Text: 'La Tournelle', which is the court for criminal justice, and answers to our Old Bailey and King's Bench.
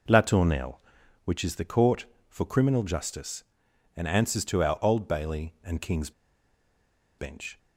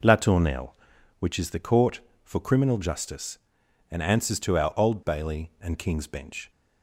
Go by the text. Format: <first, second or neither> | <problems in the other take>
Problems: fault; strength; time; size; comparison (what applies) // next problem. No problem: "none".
second | pauses between "King's" and "Bench"; at 6.1 s; 1.0 s long